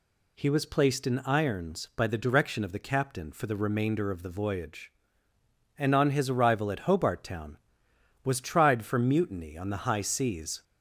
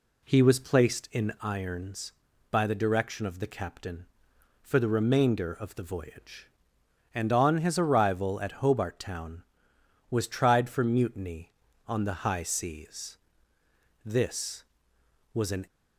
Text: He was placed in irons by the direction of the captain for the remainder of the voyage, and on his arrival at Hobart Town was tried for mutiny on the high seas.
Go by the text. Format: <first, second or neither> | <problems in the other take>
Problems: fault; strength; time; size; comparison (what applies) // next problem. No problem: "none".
first | goes on to say "This was an"; from 14.0 s on; 1.6 s long